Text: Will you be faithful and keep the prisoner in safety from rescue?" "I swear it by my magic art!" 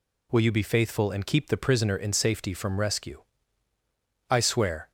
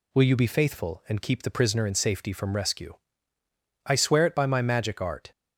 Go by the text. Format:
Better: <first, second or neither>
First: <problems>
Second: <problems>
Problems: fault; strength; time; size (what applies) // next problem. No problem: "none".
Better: second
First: stops before "it by my magic art"; at 4.8 s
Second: none